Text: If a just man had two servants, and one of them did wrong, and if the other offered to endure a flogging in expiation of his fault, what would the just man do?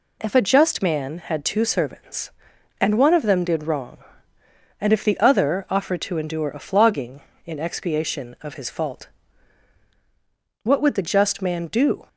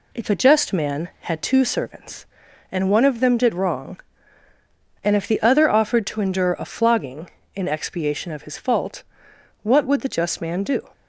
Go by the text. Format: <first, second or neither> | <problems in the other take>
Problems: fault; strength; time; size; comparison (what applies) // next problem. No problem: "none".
neither | none